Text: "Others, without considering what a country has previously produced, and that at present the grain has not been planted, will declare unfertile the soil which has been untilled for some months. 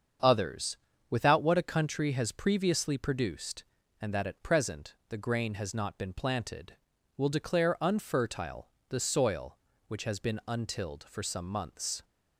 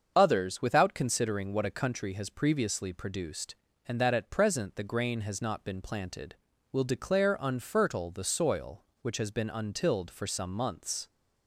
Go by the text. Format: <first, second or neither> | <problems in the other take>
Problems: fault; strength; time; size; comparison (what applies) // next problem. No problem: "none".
second | starts louder than the rest; strong; until 1.5 s; 7.5 dB; also in the second // skips "considering"; at 1.4 s // pauses between "unfertile" and "the"; slight; at 8.6 s; 0.20 s long